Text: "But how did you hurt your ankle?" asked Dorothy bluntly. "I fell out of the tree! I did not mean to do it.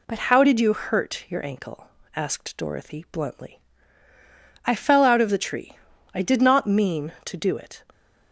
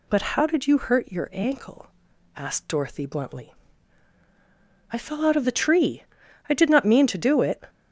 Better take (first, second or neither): neither